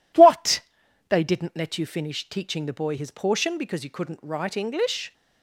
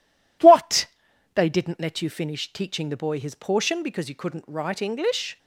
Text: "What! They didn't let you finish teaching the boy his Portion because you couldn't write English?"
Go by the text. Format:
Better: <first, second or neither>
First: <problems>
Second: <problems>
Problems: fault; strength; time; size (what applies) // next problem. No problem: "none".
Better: neither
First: none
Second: none